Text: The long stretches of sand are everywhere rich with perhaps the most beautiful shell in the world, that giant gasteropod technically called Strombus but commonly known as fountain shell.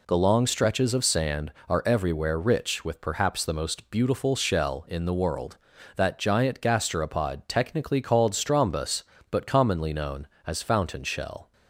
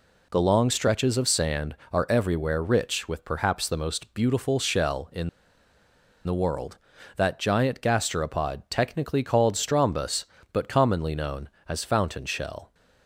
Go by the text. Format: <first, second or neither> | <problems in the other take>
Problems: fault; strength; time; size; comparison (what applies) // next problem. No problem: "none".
first | pauses between "in" and "the"; noticeable; at 5.2 s; 0.96 s long